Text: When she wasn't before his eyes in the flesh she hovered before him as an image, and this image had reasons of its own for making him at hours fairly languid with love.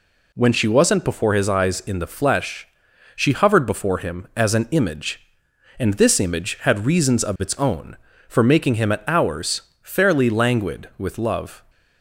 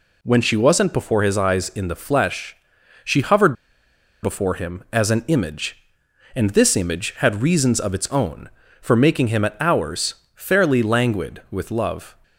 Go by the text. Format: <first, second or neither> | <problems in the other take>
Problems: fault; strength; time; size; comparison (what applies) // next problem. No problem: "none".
first | pauses between "flesh" and "she"; noticeable; at 2.5 s; 0.50 s long; noticeable in the first // pauses between "hovered" and "before"; noticeable; at 3.5 s; 0.68 s long // pauses between "hours" and "fairly"; slight; at 10.1 s; 0.20 s long; slight in the first